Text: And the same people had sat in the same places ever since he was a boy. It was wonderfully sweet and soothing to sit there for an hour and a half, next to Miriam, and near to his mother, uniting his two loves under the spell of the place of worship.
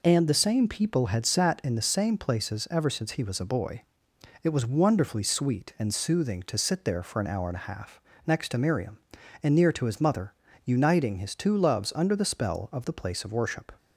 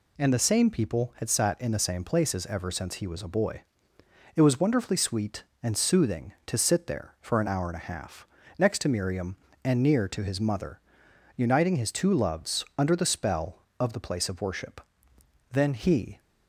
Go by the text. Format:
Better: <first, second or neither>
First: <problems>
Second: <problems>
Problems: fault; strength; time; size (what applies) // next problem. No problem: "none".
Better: first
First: none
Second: goes on to say "Then he"; noticeable; from 15.5 s on; 0.68 s long